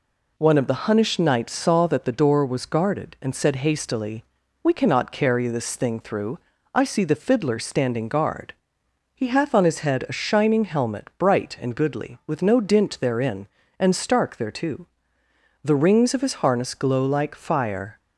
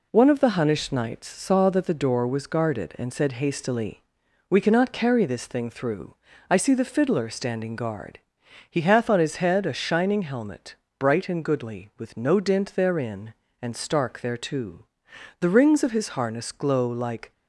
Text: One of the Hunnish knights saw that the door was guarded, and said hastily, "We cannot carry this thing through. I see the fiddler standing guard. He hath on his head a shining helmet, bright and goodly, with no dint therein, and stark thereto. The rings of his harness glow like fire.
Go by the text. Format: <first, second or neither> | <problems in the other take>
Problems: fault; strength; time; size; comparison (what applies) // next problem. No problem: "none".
first | stops before "fire"; at 17.3 s